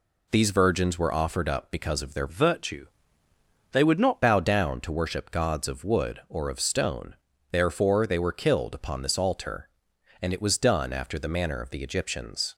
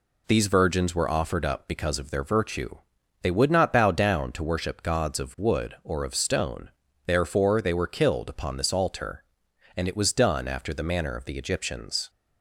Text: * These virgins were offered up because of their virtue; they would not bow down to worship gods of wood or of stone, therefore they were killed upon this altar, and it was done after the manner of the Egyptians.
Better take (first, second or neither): second